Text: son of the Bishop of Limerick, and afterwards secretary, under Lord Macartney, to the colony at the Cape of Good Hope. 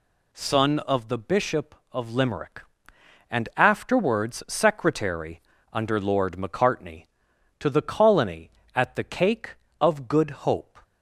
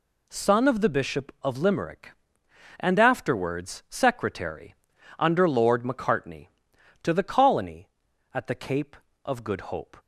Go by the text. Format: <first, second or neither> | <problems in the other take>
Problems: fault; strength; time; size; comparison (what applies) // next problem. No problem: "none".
second | says "Cake" for "Cape"; at 9.0 s